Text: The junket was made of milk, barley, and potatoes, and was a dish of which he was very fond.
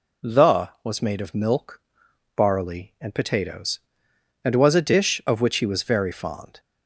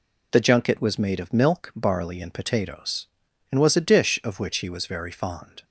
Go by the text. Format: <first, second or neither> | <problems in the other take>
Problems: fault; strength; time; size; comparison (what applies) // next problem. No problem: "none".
second | skips "junket"; at 0.7 s